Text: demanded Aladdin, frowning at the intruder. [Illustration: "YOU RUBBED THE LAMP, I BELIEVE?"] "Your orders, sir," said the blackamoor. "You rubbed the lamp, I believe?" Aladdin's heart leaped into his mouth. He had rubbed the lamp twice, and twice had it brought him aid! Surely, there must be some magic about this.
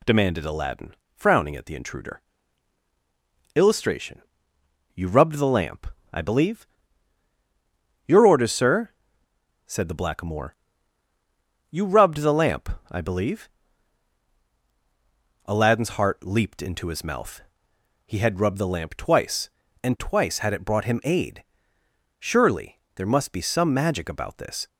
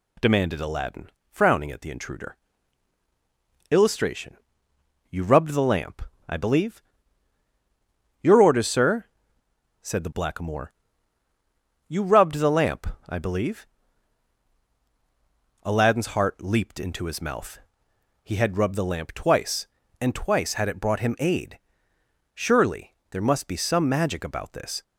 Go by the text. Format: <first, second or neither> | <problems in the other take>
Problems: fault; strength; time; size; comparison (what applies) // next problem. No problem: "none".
neither | none